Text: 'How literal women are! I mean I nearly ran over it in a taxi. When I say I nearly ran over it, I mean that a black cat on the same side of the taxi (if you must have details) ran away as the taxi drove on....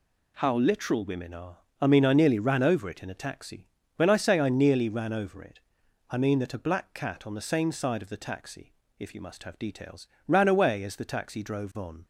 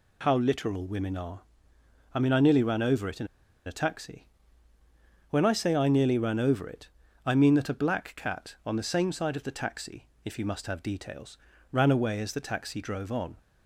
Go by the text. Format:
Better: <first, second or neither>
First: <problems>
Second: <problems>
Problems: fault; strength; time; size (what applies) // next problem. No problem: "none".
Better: first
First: none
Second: pauses between "in" and "a"; at 3.2 s; 0.40 s long